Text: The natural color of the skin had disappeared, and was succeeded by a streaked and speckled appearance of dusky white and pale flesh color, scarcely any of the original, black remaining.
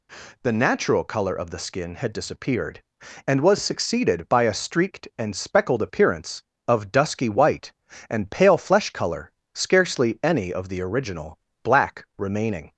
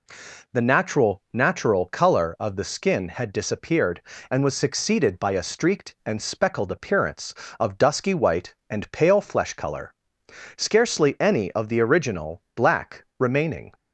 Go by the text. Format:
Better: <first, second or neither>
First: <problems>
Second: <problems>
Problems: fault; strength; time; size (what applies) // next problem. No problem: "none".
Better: first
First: none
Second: says "natural" twice; at 1.3 s